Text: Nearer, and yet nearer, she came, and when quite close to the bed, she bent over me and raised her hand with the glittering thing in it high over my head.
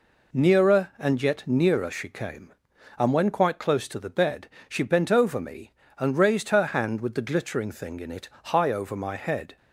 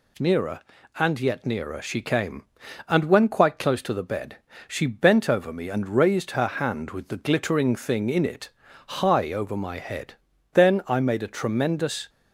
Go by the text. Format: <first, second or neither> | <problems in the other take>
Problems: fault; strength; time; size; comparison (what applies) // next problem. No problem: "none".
first | pauses between "it" and "high"; at 8.4 s; 0.38 s long; slight in the first // goes on to say "Then I made a tremendous"; from 10.5 s on; 1.5 s long